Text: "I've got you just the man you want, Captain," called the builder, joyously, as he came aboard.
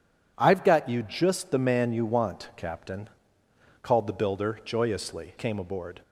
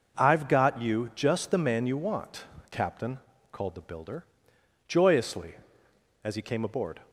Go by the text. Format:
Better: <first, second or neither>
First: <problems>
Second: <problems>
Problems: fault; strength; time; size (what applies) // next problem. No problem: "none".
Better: second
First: skips "as he"; at 5.3 s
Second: none